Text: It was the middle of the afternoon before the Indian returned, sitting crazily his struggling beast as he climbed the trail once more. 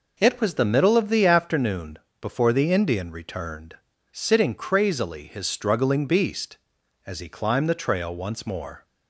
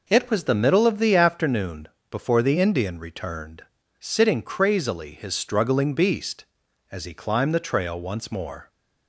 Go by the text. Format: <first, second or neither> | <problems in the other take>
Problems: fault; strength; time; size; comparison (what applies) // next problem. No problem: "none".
neither | pauses between "afternoon" and "before"; slight; the same in both